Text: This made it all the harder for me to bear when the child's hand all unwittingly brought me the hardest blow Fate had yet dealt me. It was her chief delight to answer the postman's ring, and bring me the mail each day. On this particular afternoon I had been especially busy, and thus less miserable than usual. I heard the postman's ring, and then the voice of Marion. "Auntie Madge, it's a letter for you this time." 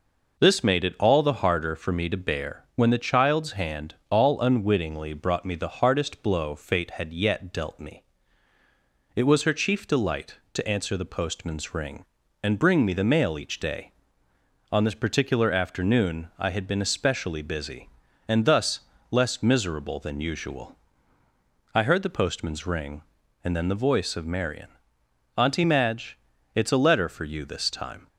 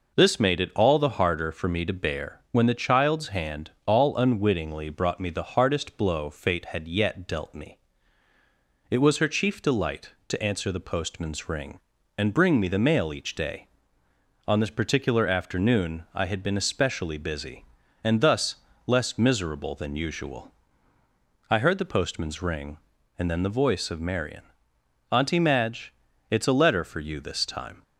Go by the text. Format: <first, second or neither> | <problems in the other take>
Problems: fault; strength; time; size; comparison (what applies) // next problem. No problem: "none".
neither | pauses between "thus" and "less"; slight; the same in both